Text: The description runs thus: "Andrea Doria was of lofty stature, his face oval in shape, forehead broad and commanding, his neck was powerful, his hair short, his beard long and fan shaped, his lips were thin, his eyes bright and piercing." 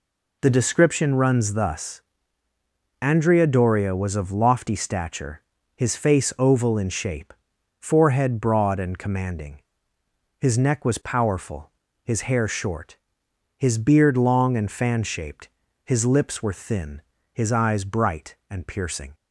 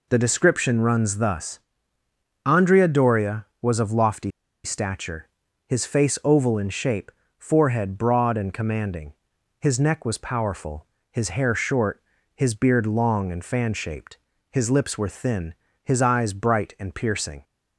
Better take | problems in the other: first | pauses between "lofty" and "stature"; slight; at 4.2 s; 0.34 s long

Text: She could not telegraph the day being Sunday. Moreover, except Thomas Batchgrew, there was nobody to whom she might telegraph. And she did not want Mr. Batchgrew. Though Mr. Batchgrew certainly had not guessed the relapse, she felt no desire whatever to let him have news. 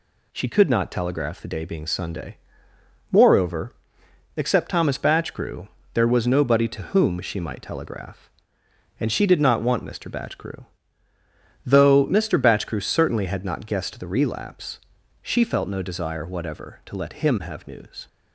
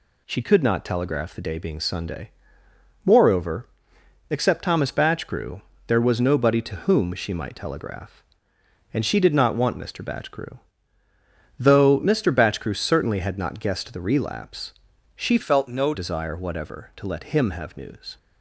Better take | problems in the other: first | changes voice from "felt" to "no"; from 15.4 to 15.9 s; 0.5 s long

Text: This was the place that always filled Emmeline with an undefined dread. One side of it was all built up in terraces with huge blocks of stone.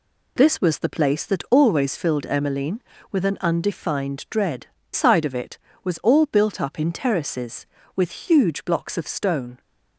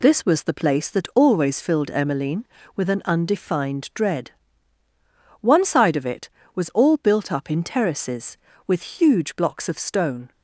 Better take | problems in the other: second | skips "One"; at 4.8 s

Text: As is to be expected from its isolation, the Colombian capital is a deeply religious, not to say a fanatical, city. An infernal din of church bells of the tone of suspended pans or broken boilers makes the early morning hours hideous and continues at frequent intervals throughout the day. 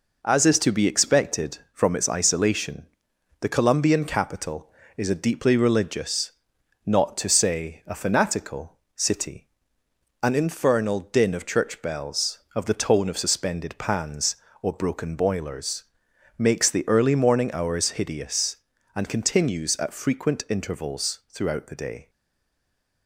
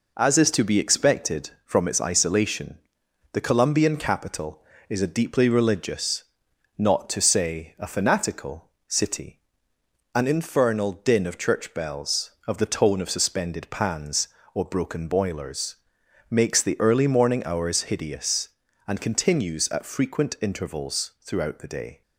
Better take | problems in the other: second | pauses between "boilers" and "makes"; noticeable; at 15.8 s; 0.54 s long; noticeable in the second // stays silent after the last word; from 22.0 s on; 1.0 s long

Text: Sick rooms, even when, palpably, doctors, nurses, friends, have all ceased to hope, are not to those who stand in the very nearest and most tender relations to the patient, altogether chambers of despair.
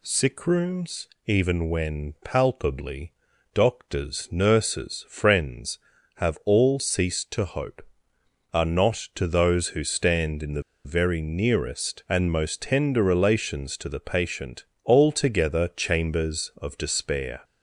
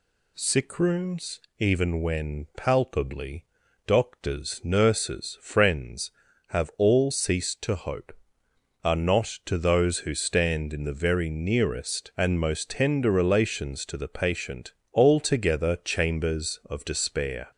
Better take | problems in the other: second | pauses between "the" and "very"; slight; at 10.6 s; 0.23 s long

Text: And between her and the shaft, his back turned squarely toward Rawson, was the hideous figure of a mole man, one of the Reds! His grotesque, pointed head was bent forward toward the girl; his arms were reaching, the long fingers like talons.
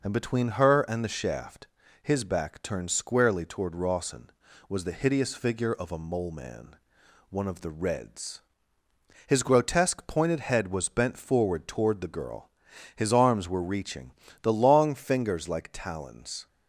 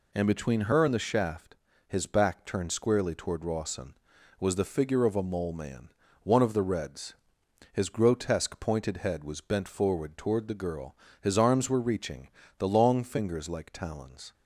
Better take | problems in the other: first | skips "hideous"; at 4.6 s

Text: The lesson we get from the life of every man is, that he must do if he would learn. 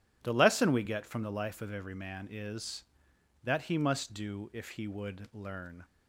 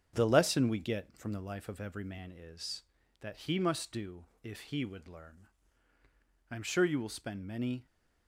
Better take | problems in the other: first | starts louder than the rest; strong; until 1.1 s; 7.5 dB // pauses between "do" and "if"; slight; at 4.2 s; 0.18 s long // goes on to say "I am sure you will spend many"; from 6.5 s on; 1.3 s long

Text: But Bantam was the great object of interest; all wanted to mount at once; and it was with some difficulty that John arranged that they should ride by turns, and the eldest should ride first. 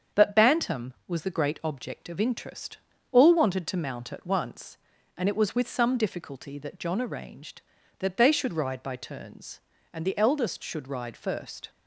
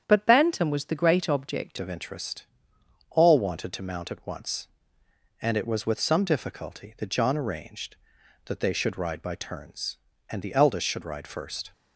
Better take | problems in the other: first | starts louder than the rest; strong; until 1.0 s; 8.5 dB; also in the first // changes voice at "of"; from 1.7 s on; 10.0 s long

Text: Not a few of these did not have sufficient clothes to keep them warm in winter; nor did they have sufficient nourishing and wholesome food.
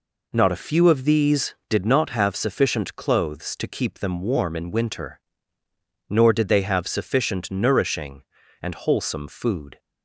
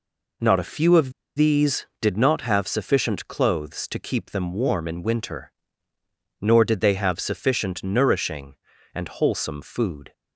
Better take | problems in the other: first | pauses between "of" and "these"; slight; at 1.1 s; 0.24 s long

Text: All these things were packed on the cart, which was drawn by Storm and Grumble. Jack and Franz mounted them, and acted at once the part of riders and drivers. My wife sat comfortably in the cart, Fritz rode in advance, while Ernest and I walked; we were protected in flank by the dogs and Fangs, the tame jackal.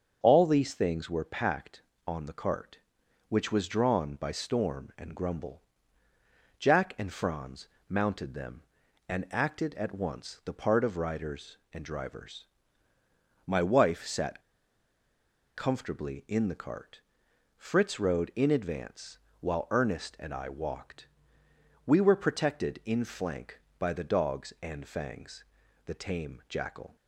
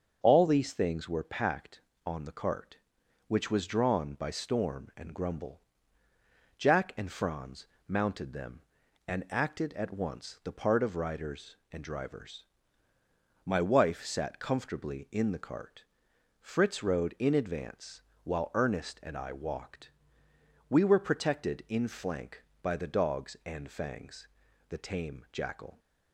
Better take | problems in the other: second | starts louder than the rest; until 1.2 s; 7 dB; also in the second // pauses between "Franz" and "mounted"; slight; at 7.6 s; 0.22 s long; slight in the second // pauses between "sat" and "comfortably"; at 14.4 s; 1.1 s long

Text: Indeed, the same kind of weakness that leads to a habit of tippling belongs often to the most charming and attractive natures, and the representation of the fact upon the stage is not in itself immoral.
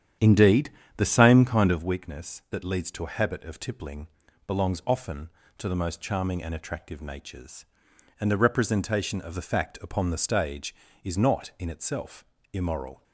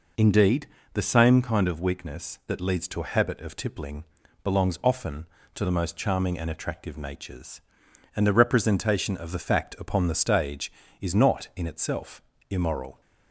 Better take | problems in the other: second | starts louder than the rest; strong; until 1.9 s; 9.5 dB // pauses between "tippling" and "belongs"; at 4.0 s; 0.38 s long; also in the second // pauses between "itself" and "immoral"; slight; at 12.2 s; 0.26 s long; slight in the second

